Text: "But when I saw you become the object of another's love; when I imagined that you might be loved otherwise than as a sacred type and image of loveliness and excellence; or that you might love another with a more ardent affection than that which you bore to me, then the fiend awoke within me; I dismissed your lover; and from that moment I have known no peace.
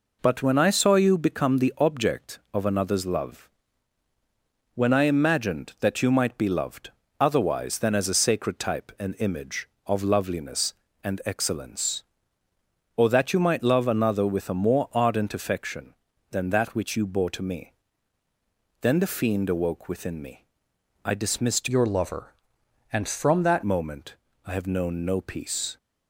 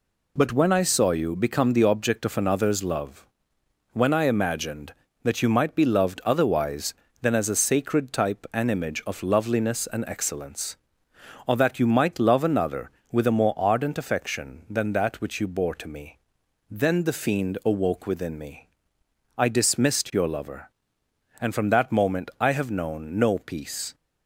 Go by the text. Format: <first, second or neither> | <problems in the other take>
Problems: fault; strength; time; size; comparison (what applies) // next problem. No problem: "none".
second | pauses between "loved" and "otherwise"; slight; at 6.9 s; 0.28 s long // changes voice from "your" to "that"; from 21.6 to 23.6 s; 2.0 s long // pauses between "moment" and "I"; slight; at 24.1 s; 0.30 s long